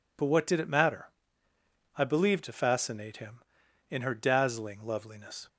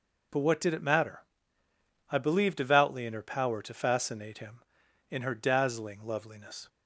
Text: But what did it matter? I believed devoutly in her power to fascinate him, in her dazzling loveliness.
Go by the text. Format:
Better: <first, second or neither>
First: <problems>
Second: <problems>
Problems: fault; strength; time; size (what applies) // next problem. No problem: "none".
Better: second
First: skips "devoutly in her power"; at 2.4 s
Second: none